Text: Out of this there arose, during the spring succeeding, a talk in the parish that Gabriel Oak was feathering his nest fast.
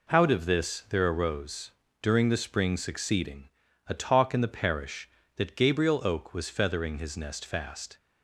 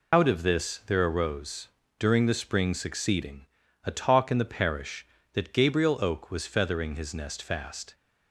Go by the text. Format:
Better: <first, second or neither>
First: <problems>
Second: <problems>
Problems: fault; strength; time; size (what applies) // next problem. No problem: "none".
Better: first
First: none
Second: loses the start of "Out"; at 0.1 s; 65 ms